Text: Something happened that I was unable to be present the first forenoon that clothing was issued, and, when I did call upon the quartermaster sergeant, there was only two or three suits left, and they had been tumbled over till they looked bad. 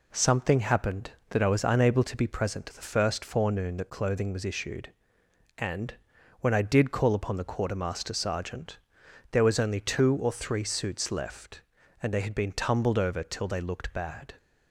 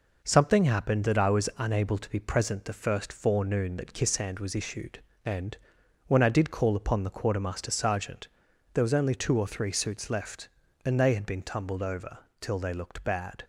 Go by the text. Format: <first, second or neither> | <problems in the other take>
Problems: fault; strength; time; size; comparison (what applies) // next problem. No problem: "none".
first | says "kissand" for "clothing"; at 3.9 s // pauses between "over" and "till"; slight; at 12.1 s; 0.22 s long